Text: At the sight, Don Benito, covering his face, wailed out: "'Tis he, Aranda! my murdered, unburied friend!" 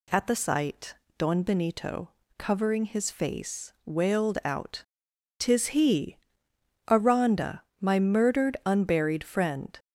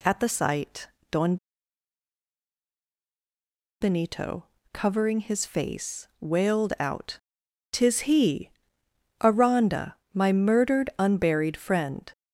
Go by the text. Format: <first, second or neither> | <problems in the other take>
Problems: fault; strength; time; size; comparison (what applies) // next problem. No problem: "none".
first | pauses between "Don" and "Benito"; strong; at 1.3 s; 2.4 s long